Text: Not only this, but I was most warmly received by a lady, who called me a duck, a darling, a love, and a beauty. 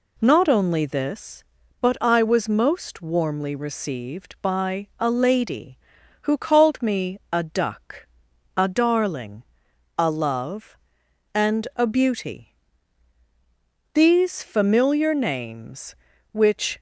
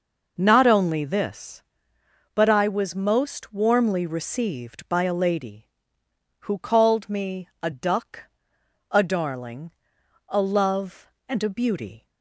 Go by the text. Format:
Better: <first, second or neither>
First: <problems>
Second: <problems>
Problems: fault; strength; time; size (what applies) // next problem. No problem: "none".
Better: second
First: goes on to say "These familiar names which"; strong; from 13.9 s on; 2.8 s long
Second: none